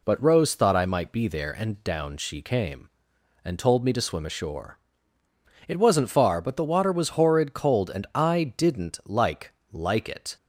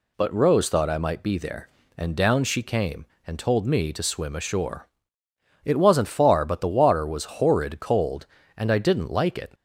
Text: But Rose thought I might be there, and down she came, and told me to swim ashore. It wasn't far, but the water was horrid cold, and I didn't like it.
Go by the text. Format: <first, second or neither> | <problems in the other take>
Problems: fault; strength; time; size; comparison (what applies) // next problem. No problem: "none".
second | says "like" twice; at 9.7 s